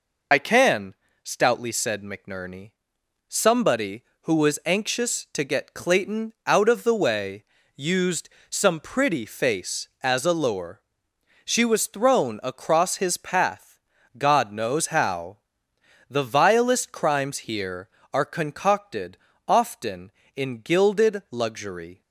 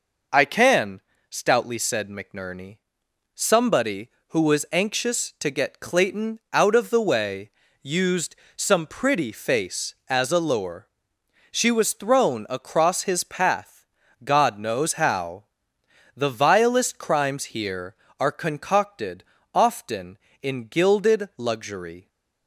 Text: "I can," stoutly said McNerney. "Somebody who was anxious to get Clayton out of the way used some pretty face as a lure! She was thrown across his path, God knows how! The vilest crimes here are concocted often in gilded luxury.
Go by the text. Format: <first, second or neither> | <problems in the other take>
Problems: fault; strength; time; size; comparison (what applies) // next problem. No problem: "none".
second | loses the start of "I"; at 0.3 s; 55 ms // pauses between "way" and "used"; slight; at 7.4 s; 0.32 s long; slight in the second // pauses between "used" and "some"; slight; at 8.2 s; 0.20 s long; slight in the second // pauses between "concocted" and "often"; slight; at 19.1 s; 0.28 s long; slight in the second